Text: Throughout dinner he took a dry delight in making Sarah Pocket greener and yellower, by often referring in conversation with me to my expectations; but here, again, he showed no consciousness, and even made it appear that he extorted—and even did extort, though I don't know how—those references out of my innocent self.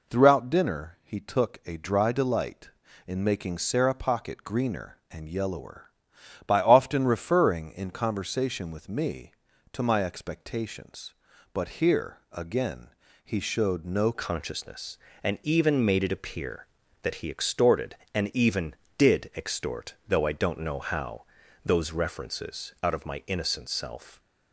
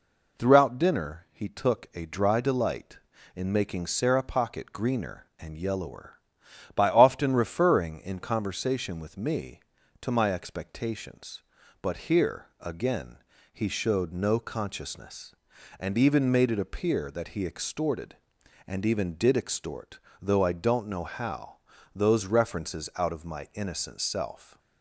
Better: second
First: changes voice at "consciousness"; from 14.1 s on; 10.0 s long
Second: none

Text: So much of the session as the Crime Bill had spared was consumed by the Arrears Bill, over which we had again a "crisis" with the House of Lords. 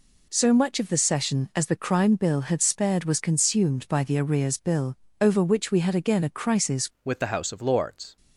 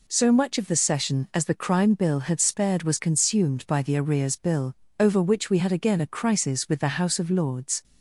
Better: second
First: changes voice at "with"; from 7.0 s on; 1.1 s long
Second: none

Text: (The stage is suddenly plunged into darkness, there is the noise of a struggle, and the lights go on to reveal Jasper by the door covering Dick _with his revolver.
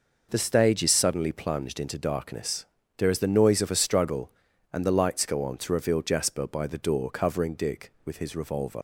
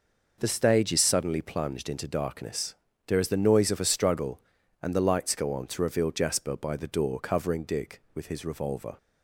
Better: second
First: leaves "revolver" unfinished; at 8.7 s; 65 ms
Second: none

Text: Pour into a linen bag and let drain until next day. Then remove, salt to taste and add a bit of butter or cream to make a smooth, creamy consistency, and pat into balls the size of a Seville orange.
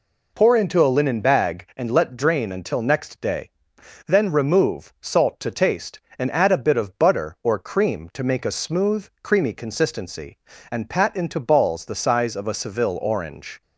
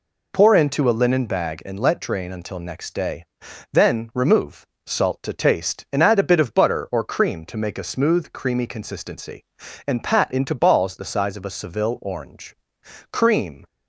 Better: first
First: none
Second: goes on to say "CREAM"; from 13.1 s on; 0.54 s long

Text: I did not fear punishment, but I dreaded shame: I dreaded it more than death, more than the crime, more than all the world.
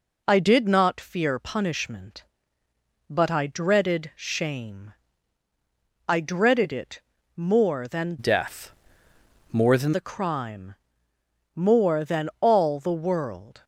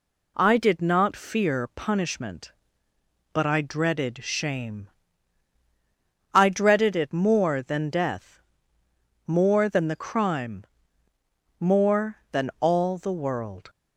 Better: second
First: pauses between "it" and "more"; slight; at 7.0 s; 0.34 s long // changes voice from "death" to "than"; from 8.1 to 9.9 s; 1.8 s long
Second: none

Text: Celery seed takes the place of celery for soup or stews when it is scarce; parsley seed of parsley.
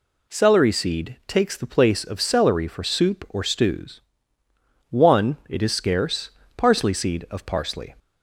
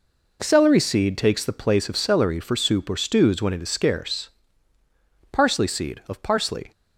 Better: second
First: says "one" for "when"; at 4.9 s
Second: none

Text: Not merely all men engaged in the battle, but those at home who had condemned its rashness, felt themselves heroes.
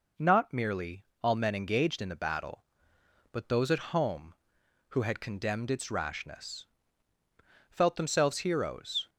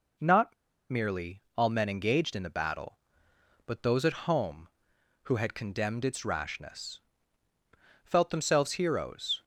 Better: first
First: pauses between "merely" and "all"; slight; at 1.0 s; 0.19 s long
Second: pauses between "Not" and "merely"; at 0.5 s; 0.37 s long // pauses between "merely" and "all"; slight; at 1.4 s; 0.16 s long

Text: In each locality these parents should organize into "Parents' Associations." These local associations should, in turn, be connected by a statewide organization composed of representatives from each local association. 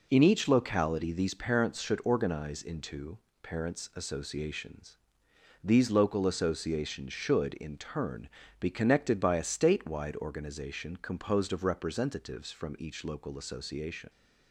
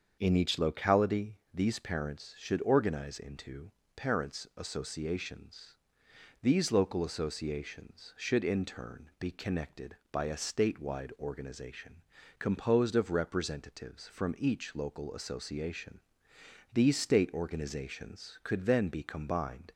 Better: first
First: pauses between "into" and "Parents"; slight; at 3.1 s; 0.24 s long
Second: starts louder than the rest; until 1.2 s; 7 dB // pauses between "locality" and "these"; slight; at 1.3 s; 0.18 s long // pauses between "into" and "Parents"; slight; at 3.6 s; 0.24 s long // pauses between "organization" and "composed"; at 12.0 s; 0.38 s long // goes on to say "These state organizations could then be combined"; strong; from 16.7 s on; 2.9 s long

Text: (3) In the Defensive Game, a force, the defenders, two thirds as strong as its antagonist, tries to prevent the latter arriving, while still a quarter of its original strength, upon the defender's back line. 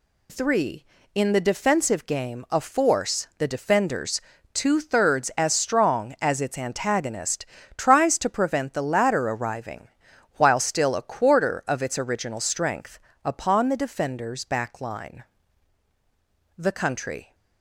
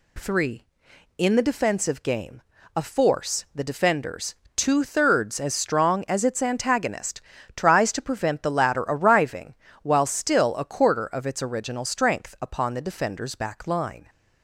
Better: second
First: goes on to say "The Country"; noticeable; from 16.5 s on; 0.78 s long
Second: none

